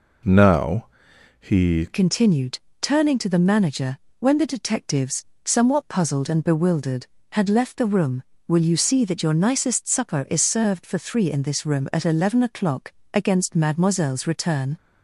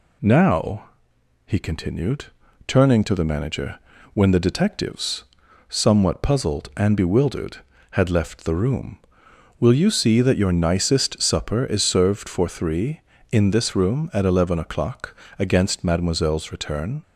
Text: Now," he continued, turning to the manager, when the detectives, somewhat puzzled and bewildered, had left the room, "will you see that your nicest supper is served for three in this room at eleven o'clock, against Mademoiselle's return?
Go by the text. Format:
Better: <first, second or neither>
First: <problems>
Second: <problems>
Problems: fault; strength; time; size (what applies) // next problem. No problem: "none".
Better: second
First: changes voice at "continued"; from 1.9 s on; 12.8 s long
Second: none